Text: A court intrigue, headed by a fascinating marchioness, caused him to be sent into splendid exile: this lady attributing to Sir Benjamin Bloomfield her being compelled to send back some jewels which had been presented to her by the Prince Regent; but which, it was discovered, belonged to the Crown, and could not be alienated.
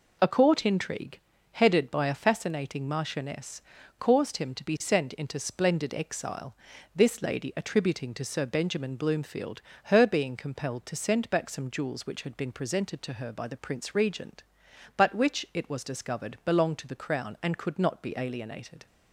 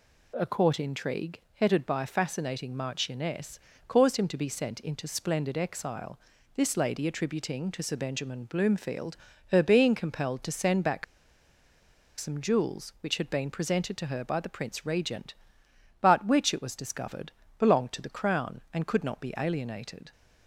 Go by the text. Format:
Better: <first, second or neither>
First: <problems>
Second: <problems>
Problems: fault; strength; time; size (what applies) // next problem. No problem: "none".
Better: first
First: pauses between "Bloomfield" and "her"; slight; at 9.6 s; 0.24 s long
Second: pauses between "Bloomfield" and "her"; at 9.1 s; 0.38 s long // pauses between "back" and "some"; at 11.0 s; 1.1 s long